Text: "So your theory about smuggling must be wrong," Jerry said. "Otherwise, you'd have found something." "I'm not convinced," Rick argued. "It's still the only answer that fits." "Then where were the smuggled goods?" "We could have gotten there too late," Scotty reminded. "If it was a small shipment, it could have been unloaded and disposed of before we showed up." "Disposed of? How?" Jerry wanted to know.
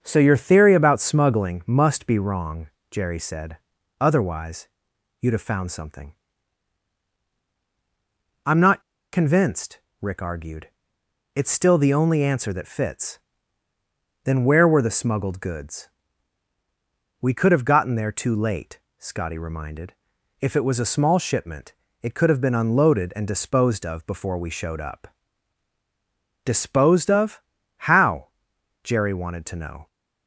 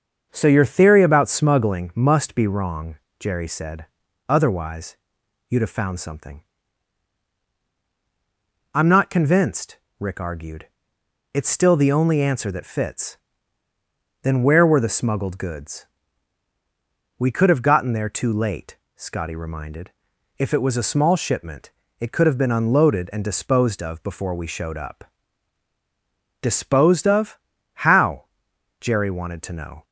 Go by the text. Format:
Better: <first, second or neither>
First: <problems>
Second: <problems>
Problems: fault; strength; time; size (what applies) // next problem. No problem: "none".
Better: second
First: starts louder than the rest; until 1.0 s; 7 dB // pauses between "not" and "convinced"; slight; at 8.8 s; 0.32 s long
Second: starts louder than the rest; until 1.3 s; 7 dB